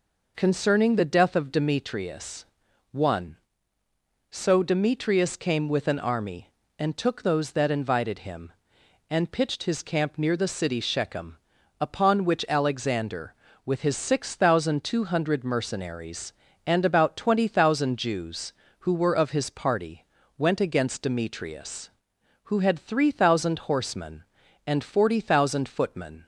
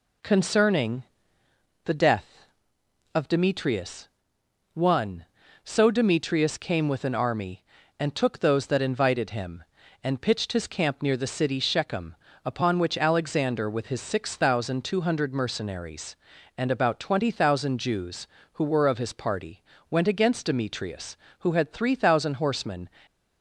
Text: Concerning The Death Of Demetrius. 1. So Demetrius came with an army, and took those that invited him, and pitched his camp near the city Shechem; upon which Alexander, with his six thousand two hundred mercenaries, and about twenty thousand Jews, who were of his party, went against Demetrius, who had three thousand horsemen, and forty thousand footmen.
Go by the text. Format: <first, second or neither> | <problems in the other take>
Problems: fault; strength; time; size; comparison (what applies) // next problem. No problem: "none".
first | pauses between "Concerning" and "The"; noticeable; at 1.0 s; 0.80 s long // stops before "and forty thousand footmen"; at 23.0 s